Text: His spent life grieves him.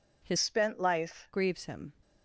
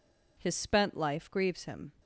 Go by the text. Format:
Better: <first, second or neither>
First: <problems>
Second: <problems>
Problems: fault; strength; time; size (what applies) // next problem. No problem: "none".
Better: second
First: changes voice from "spent" to "life"; from 0.3 to 1.2 s; 0.9 s long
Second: none